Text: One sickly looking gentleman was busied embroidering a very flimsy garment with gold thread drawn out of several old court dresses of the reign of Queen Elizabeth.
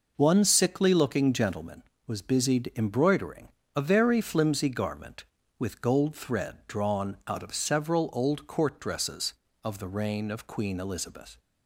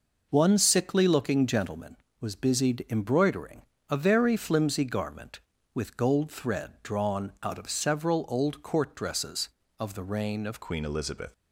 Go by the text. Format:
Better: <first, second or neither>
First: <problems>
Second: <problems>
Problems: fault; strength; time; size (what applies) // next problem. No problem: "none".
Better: first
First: pauses between "embroidering" and "a"; slight; at 3.4 s; 0.27 s long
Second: pauses between "embroidering" and "a"; slight; at 3.6 s; 0.26 s long // changes voice at "Queen"; from 10.6 s on; 0.7 s long